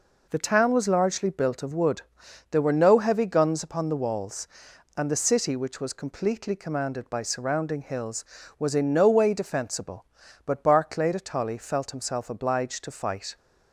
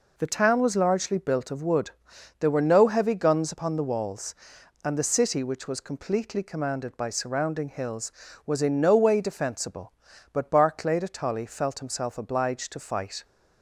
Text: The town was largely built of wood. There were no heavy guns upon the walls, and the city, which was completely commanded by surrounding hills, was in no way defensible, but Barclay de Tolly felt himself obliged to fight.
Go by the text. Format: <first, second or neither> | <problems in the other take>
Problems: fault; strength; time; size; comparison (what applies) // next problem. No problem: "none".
neither | none